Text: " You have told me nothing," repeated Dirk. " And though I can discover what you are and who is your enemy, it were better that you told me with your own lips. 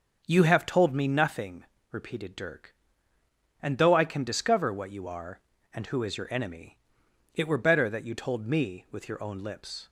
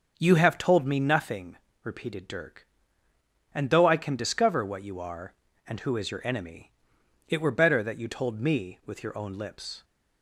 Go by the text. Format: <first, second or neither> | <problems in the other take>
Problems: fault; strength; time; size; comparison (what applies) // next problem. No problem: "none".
neither | starts louder than the rest; noticeable; the same in both